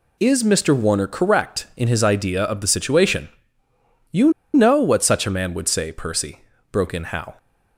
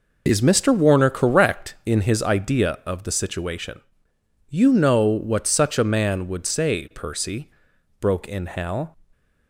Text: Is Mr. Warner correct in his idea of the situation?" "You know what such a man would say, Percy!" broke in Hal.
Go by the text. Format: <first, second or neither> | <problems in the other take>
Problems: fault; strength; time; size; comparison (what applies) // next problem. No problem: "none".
second | pauses between "You" and "know"; slight; at 4.3 s; 0.22 s long